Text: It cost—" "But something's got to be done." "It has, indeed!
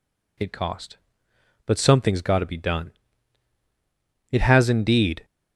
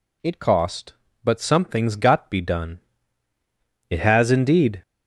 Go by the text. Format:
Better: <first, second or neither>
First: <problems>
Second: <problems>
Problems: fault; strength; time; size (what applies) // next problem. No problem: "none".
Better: first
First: none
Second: skips "to"; at 2.2 s